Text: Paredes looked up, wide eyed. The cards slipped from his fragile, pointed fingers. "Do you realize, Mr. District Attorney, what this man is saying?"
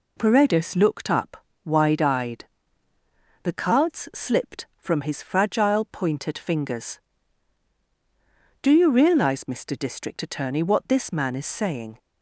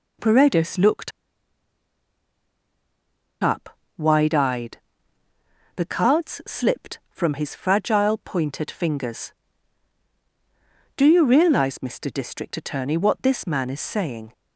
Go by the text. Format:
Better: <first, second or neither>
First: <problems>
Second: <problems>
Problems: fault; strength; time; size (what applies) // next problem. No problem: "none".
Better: first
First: none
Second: pauses between "looked" and "up"; strong; at 1.1 s; 2.3 s long